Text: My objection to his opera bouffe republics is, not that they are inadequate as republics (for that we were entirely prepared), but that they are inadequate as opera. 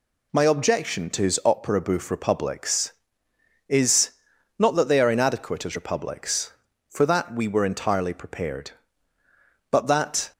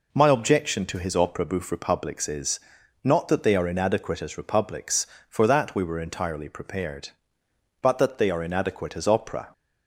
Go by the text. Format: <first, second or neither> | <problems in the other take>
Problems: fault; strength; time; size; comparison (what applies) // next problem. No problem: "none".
second | stops before "they are inadequate as opera"; at 10.3 s